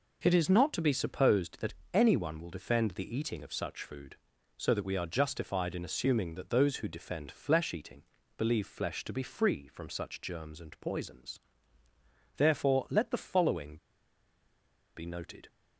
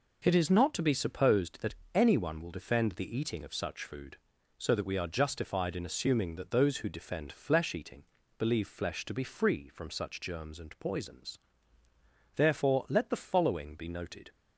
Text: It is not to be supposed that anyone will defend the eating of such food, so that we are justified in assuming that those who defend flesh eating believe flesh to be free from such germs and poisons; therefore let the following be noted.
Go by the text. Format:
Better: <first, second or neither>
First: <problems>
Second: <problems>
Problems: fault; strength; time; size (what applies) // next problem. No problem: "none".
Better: second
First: pauses between "that" and "anyone"; slight; at 1.7 s; 0.18 s long // pauses between "eating" and "believe"; slight; at 8.0 s; 0.34 s long // pauses between "following" and "be"; at 13.7 s; 1.1 s long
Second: pauses between "that" and "anyone"; slight; at 1.7 s; 0.18 s long // pauses between "eating" and "believe"; slight; at 8.0 s; 0.34 s long